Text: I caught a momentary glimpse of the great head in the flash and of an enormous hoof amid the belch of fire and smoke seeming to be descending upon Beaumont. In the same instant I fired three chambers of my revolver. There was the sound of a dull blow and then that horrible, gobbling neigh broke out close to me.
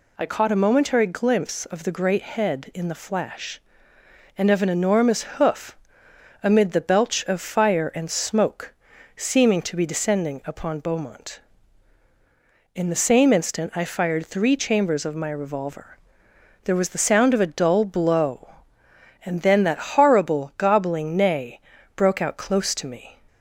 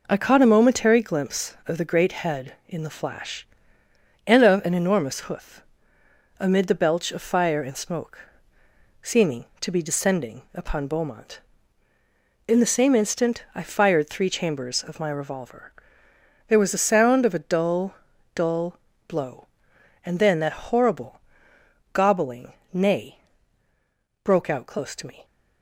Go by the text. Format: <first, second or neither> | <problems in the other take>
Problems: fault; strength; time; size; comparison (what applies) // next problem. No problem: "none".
first | pauses between "hoof" and "amid"; noticeable; at 5.6 s; 0.76 s long; noticeable in the first // pauses between "smoke" and "seeming"; noticeable; at 8.1 s; 0.82 s long; also in the first // says "dull" twice; at 18.3 s // pauses between "gobbling" and "neigh"; slight; at 22.5 s; 0.18 s long // pauses between "neigh" and "broke"; at 23.2 s; 1.0 s long; slight in the first